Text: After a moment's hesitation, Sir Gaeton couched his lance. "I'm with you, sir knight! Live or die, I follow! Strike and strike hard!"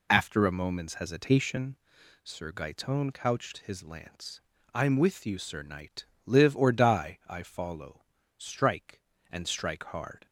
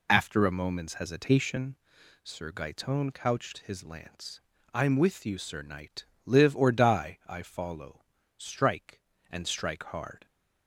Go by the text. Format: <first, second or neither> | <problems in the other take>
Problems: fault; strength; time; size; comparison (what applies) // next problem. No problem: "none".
neither | none